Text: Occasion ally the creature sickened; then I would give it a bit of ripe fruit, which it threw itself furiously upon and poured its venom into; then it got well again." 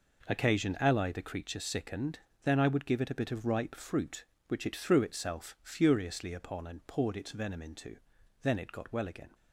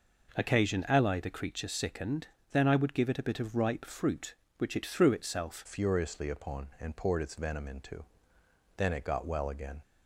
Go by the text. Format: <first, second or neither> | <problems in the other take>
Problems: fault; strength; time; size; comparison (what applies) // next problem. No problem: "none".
first | changes voice at "furiously"; from 5.6 s on; 4.2 s long